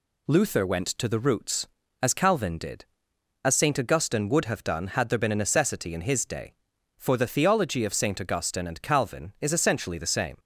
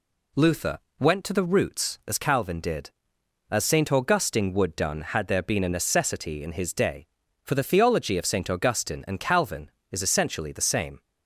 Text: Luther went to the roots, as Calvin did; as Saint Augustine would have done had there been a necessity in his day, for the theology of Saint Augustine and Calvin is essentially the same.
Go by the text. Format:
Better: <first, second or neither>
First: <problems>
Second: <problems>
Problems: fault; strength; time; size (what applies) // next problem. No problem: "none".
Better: first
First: none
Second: pauses between "Luther" and "went"; slight; at 0.7 s; 0.20 s long // skips "have"; at 4.7 s